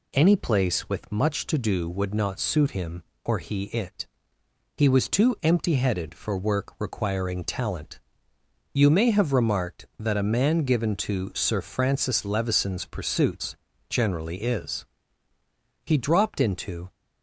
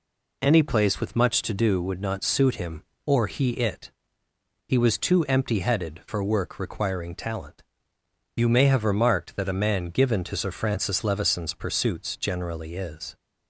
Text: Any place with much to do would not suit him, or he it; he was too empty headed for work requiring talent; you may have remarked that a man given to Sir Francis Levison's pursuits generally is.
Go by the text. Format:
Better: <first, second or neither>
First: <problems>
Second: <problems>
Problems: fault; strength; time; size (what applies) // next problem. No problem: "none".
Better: second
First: pauses between "pursuits" and "generally"; slight; at 13.5 s; 0.34 s long // goes on to say "He dropped into"; noticeable; from 15.8 s on; 1.0 s long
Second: none